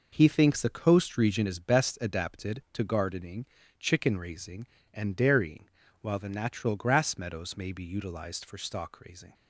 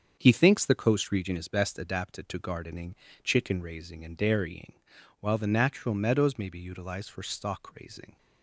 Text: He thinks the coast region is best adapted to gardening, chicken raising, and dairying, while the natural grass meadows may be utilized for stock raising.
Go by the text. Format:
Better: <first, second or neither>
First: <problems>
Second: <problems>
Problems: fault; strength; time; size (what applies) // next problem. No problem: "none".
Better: first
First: none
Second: starts louder than the rest; strong; until 1.2 s; 7 dB // skips "grass"; at 5.9 s